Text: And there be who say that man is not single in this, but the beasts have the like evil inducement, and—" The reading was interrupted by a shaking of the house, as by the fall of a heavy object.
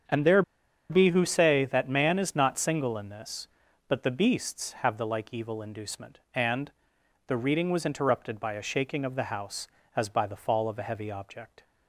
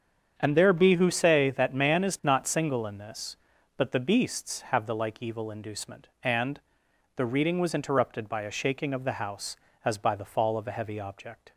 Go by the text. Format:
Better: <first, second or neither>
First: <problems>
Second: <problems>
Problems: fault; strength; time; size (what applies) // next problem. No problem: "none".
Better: second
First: starts louder than the rest; strong; until 1.5 s; 7.5 dB // pauses between "there" and "be"; noticeable; at 0.4 s; 0.48 s long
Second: starts louder than the rest; strong; until 1.3 s; 7.5 dB